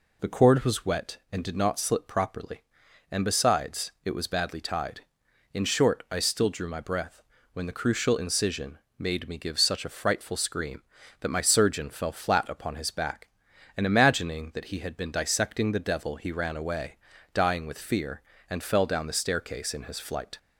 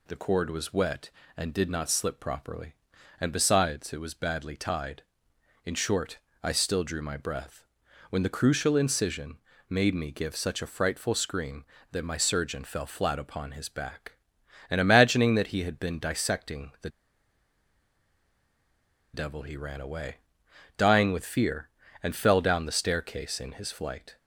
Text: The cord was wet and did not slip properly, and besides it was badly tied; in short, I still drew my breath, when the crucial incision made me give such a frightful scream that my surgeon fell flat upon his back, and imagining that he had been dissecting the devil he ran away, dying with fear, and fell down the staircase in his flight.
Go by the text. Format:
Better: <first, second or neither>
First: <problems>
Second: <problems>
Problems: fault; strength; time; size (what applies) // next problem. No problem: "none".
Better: first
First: pauses between "incision" and "made"; slight; at 8.7 s; 0.18 s long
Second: pauses between "incision" and "made"; slight; at 9.3 s; 0.30 s long // pauses between "the" and "devil"; strong; at 16.8 s; 2.2 s long